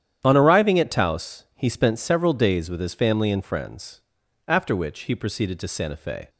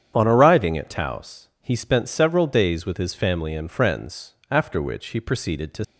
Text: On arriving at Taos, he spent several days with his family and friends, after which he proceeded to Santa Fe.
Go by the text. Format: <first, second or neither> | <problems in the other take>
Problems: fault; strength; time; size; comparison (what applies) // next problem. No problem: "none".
first | starts louder than the rest; strong; until 1.1 s; 8.5 dB; strong in the first // stops before "Santa Fe"; at 5.8 s